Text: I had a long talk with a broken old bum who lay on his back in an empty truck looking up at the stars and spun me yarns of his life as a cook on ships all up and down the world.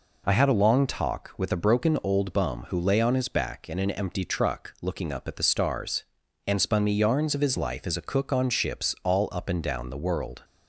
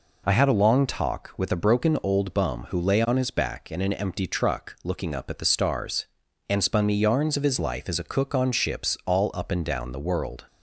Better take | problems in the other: neither | none

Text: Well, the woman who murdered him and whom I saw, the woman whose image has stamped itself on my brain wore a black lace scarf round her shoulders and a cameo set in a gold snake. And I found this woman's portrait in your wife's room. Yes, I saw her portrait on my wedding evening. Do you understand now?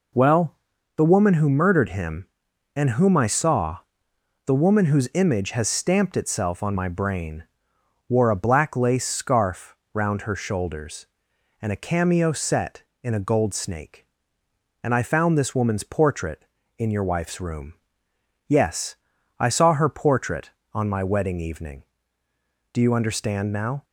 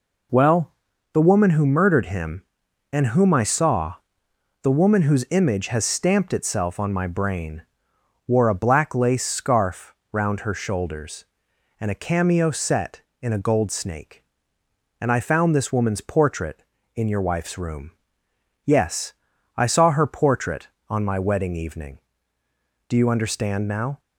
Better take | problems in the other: neither | pauses between "brain" and "wore"; noticeable; the same in both // pauses between "scarf" and "round"; slight; the same in both

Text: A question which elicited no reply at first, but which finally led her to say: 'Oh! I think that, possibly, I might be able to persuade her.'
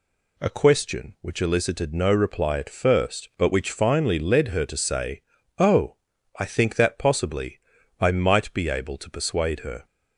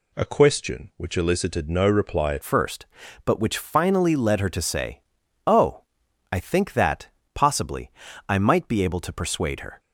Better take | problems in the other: first | changes voice at "first"; from 2.4 s on; 7.3 s long

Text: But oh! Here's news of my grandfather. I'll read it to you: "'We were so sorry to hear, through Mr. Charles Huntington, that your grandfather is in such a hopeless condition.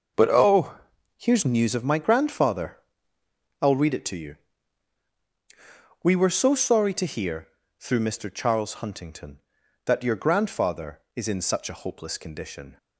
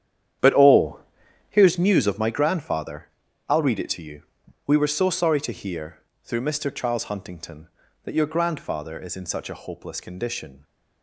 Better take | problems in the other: first | starts louder than the rest; strong; until 1.8 s; 10 dB

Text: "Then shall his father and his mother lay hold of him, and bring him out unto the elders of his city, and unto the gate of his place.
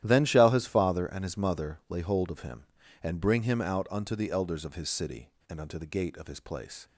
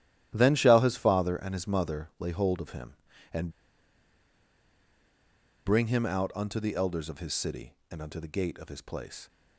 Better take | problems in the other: first | starts louder than the rest; strong; until 1.3 s; 12 dB; strong in the first // pauses between "and" and "bring"; strong; at 3.5 s; 2.1 s long

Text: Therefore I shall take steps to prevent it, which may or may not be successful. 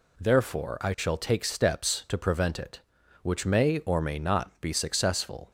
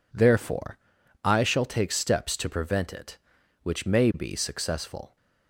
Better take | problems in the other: first | pauses between "Therefore" and "I"; noticeable; at 0.7 s; 0.46 s long // skips "or may not"; at 4.1 s

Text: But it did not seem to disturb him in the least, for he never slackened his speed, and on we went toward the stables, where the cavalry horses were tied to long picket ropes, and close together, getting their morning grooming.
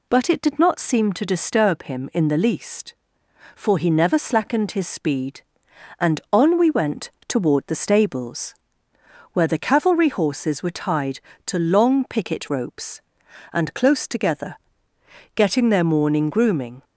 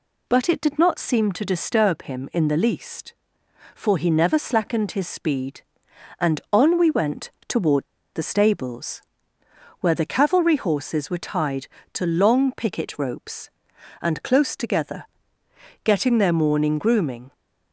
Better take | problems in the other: first | pauses between "went" and "toward"; slight; at 7.3 s; 0.16 s long; slight in the first // pauses between "toward" and "the"; slight; at 7.8 s; 0.27 s long

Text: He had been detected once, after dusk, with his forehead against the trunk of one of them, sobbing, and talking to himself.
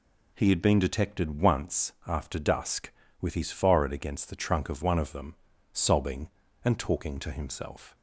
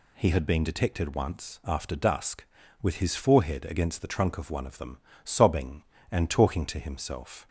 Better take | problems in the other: neither | none

